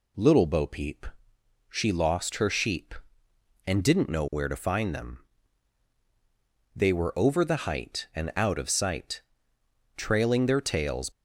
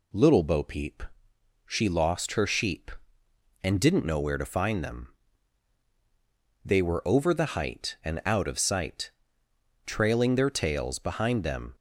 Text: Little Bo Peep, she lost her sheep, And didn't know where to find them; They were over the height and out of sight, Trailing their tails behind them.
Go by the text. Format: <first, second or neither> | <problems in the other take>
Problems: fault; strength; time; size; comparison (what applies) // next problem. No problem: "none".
second | stops before "behind them"; at 11.1 s